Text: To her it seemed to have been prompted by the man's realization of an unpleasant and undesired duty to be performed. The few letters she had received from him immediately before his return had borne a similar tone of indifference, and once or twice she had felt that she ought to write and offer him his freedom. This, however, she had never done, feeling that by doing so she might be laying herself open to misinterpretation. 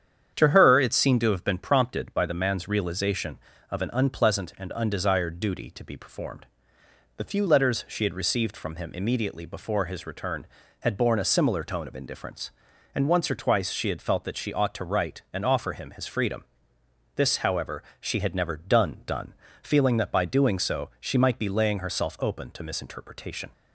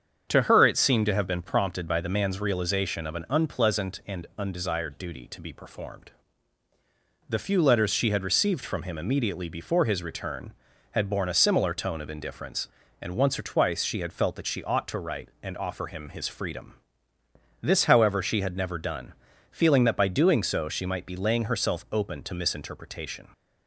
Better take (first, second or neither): second